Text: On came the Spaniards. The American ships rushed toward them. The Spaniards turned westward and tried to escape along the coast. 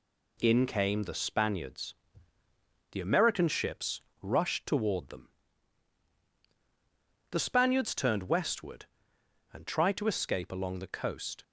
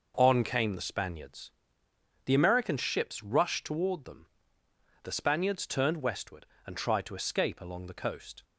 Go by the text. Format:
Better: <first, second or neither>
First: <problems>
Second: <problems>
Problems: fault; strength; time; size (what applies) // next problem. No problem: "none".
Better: second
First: says "In" for "On"; at 0.4 s // pauses between "ships" and "rushed"; slight; at 3.9 s; 0.24 s long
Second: none